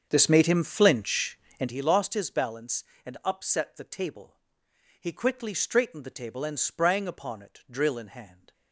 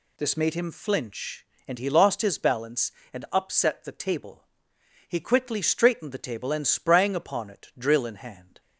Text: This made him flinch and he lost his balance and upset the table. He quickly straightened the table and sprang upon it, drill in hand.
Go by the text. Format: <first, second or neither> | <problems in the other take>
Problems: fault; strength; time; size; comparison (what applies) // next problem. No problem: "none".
second | starts louder than the rest; strong; until 1.8 s; 7.5 dB